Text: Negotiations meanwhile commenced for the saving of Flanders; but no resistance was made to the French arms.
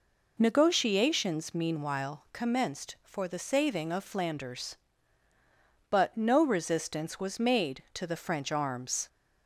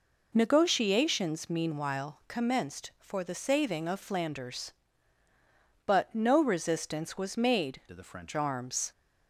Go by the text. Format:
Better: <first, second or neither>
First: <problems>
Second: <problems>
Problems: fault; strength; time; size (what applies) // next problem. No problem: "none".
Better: first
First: none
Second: changes voice from "to" to "French"; from 7.8 to 8.3 s; 0.5 s long